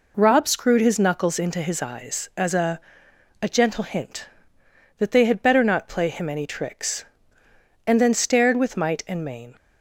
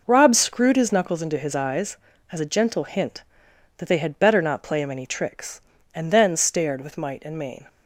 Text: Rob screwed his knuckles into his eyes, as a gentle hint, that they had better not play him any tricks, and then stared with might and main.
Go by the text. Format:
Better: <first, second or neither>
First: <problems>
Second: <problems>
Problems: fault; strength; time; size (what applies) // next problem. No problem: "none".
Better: second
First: says "a" twice; at 3.4 s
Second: none